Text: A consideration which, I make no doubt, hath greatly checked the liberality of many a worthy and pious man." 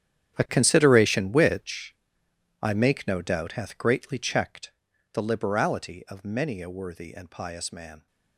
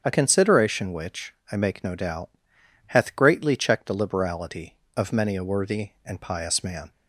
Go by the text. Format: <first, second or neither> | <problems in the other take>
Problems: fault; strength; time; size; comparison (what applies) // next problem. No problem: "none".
second | gets quieter; strong; throughout; 16.5 dB // starts louder than the rest; strong; until 1.4 s; 10 dB; strong in the second // pauses between "checked" and "the"; at 4.7 s; 0.42 s long